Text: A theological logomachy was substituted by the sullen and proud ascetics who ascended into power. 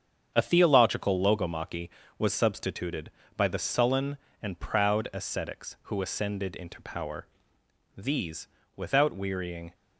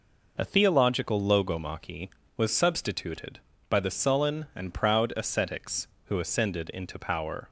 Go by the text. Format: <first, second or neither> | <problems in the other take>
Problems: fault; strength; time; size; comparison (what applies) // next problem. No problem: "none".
second | starts louder than the rest; strong; until 1.3 s; 8 dB // goes on to say "These without wearying"; strong; from 7.9 s on; 1.7 s long